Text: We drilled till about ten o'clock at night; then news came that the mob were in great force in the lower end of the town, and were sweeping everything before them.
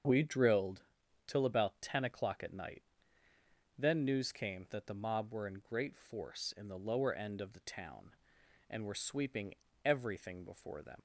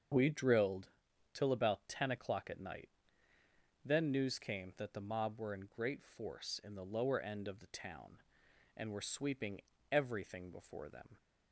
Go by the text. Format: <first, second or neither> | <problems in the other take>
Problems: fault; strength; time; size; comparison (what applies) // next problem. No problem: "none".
second | starts louder than the rest; until 1.5 s; 7 dB; also in the second // pauses between "drilled" and "till"; at 0.8 s; 0.44 s long; also in the second // pauses between "sweeping" and "everything"; slight; at 9.5 s; 0.30 s long; slight in the second // leaves "them" unfinished; at 10.9 s; 80 ms